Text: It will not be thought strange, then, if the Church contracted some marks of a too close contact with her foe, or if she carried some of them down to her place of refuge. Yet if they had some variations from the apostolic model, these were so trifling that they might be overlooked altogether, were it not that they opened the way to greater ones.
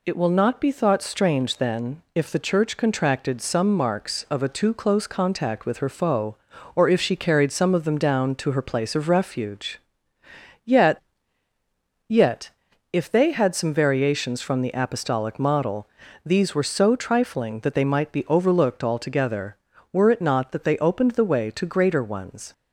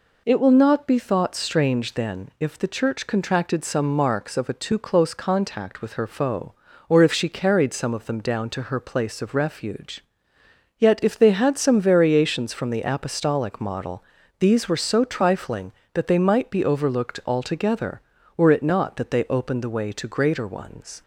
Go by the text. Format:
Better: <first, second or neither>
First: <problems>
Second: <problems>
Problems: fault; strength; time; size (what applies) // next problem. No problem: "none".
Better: second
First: says "Yet" twice; at 12.0 s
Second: none